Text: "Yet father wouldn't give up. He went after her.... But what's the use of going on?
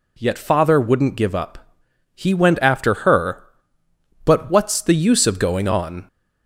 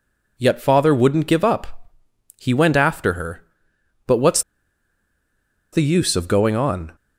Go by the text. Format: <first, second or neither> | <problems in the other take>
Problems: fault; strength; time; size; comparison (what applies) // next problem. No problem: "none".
first | pauses between "what's" and "the"; strong; at 4.4 s; 1.3 s long